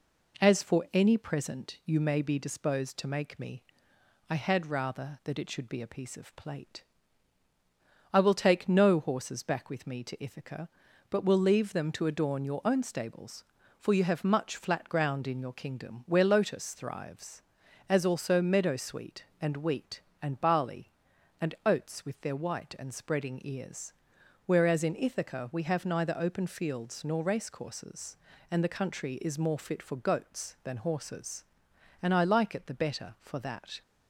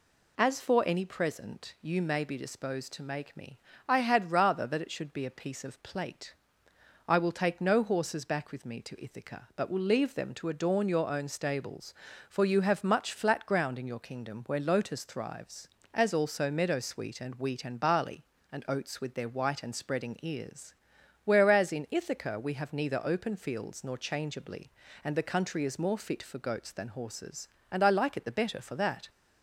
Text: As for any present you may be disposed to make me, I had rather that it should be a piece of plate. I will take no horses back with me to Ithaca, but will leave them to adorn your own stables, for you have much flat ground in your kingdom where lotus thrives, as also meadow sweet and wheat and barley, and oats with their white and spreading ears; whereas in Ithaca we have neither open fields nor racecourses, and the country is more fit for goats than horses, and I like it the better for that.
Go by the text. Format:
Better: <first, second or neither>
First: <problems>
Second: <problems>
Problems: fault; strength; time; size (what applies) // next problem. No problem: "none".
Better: first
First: none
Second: says "changeably" for "racecourses"; at 23.9 s